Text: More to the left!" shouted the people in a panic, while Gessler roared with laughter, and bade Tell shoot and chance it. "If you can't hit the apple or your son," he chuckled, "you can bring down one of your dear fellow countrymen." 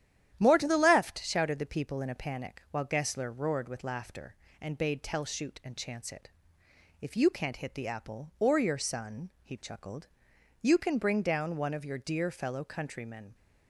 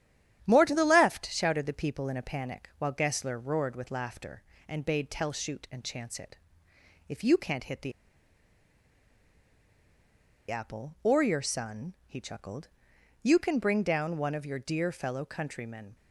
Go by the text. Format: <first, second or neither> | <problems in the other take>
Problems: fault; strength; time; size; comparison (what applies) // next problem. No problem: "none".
first | starts louder than the rest; strong; until 1.4 s; 10.5 dB; strong in the first // pauses between "the" and "apple"; strong; at 7.9 s; 2.5 s long